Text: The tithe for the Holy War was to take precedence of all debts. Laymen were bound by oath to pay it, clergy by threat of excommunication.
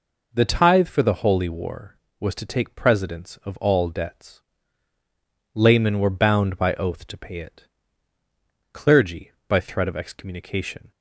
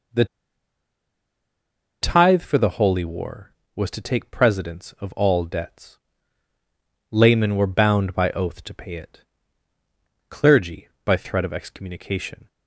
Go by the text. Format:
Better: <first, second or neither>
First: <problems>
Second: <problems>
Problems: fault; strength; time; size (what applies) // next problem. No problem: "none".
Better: first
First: none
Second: pauses between "The" and "tithe"; strong; at 0.2 s; 1.7 s long